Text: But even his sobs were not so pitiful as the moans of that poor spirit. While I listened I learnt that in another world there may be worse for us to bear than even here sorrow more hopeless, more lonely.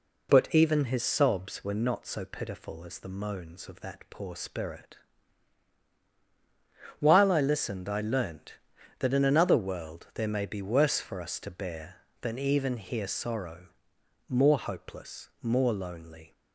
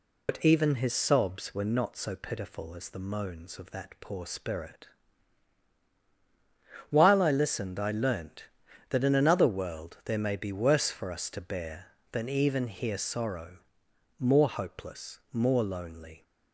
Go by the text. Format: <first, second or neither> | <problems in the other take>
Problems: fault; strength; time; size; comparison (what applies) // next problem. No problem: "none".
first | loses the start of "But"; at 0.2 s; 95 ms // pauses between "sorrow" and "more"; noticeable; at 13.5 s; 0.62 s long; noticeable in the first